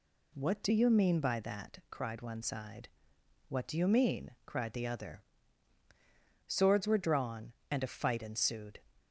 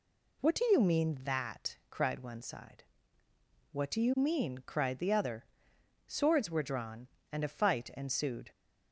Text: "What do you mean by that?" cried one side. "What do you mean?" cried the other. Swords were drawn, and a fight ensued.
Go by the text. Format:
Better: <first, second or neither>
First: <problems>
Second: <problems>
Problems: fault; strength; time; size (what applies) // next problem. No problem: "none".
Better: first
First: none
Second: skips "by"; at 1.2 s